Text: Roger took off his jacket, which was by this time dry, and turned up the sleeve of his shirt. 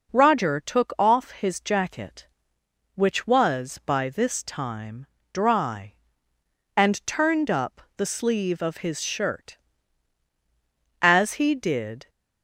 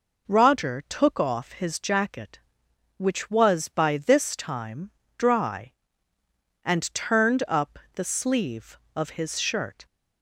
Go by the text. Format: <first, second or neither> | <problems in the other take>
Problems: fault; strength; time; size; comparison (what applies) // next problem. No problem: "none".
second | pauses between "time" and "dry"; slight; at 5.0 s; 0.28 s long; slight in the second // pauses between "up" and "the"; slight; at 7.8 s; 0.16 s long; slight in the second // goes on to say "As he did"; noticeable; from 11.0 s on; 1.0 s long